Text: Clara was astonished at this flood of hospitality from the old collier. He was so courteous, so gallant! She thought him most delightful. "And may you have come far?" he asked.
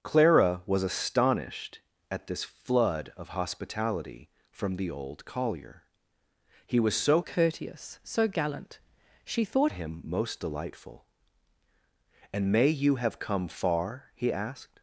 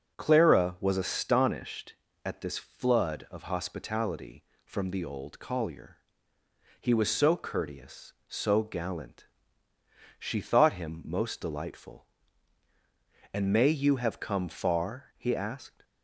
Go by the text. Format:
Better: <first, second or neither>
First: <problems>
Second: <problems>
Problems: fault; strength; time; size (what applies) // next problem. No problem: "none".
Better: second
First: starts louder than the rest; until 1.0 s; 7 dB // changes voice from "courteous" to "thought"; from 7.2 to 9.7 s; 2.5 s long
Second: none